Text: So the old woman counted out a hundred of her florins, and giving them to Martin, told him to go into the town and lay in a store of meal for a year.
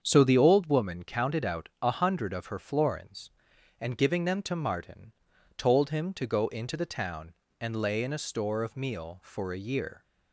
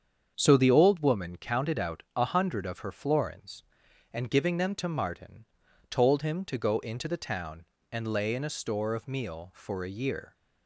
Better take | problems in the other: neither | starts louder than the rest; strong; the same in both

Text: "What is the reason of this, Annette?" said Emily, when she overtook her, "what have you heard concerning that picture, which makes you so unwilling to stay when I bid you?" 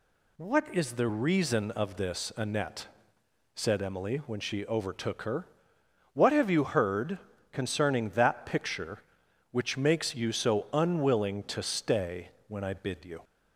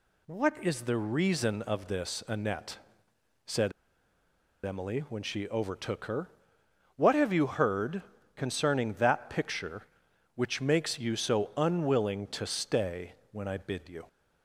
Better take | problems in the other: first | pauses between "said" and "Emily"; noticeable; at 3.7 s; 0.94 s long // pauses between "heard" and "concerning"; slight; at 8.0 s; 0.32 s long; slight in the first // pauses between "stay" and "when"; slight; at 13.1 s; 0.18 s long; slight in the first

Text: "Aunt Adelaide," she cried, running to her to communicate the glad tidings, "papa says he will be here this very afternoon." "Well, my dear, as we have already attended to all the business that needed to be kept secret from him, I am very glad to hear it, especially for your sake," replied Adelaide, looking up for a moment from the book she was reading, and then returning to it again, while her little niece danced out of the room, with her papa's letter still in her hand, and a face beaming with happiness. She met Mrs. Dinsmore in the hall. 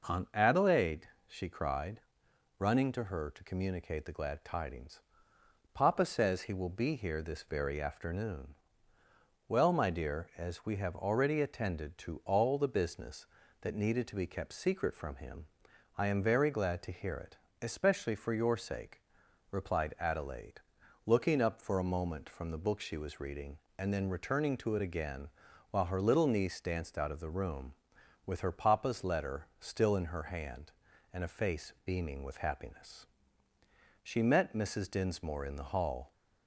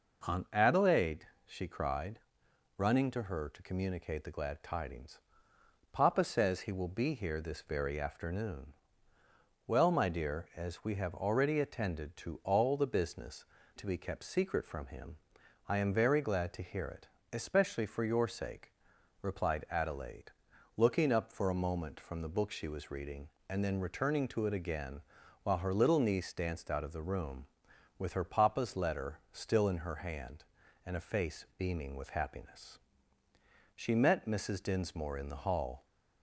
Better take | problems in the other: first | skips "that needed"; at 13.6 s

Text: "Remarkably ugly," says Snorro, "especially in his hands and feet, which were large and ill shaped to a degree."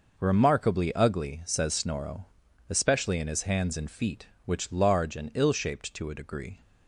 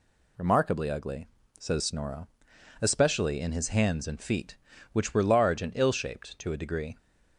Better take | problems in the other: second | skips "were"; at 4.7 s

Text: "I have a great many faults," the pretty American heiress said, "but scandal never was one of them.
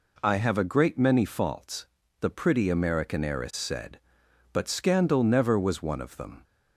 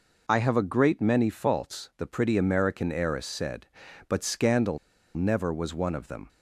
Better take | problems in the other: first | pauses between "scandal" and "never"; at 4.7 s; 0.37 s long

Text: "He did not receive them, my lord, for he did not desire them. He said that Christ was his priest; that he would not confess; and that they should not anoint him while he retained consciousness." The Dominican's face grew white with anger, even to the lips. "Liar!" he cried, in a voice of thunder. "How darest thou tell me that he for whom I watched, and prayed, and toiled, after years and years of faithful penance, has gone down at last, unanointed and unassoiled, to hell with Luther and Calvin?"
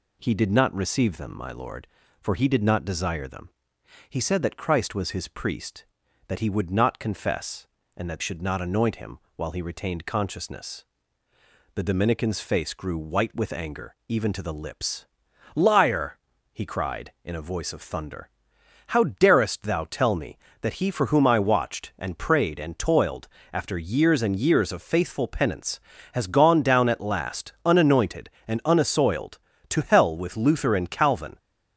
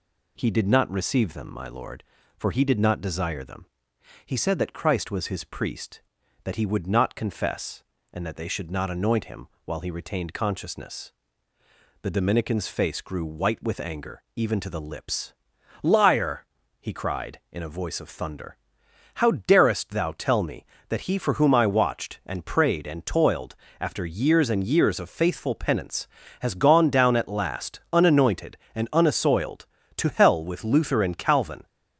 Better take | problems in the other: second | skips "they"; at 8.2 s // pauses between "him" and "while"; slight; at 9.1 s; 0.16 s long; slight in the second

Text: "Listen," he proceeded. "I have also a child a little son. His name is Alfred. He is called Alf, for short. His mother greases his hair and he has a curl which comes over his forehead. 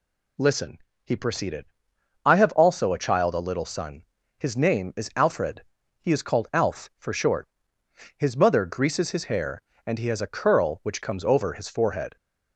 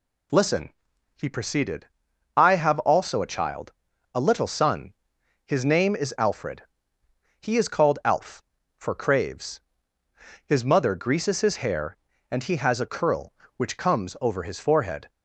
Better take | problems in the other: first | pauses between "child" and "a"; at 3.7 s; 0.42 s long // says "craves" for "short"; at 8.9 s

